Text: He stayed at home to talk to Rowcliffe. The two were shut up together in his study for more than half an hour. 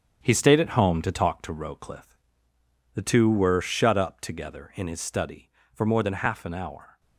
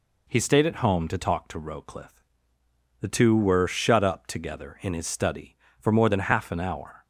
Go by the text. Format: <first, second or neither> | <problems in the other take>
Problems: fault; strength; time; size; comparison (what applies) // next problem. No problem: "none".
second | gets quieter; strong; throughout; 7.5 dB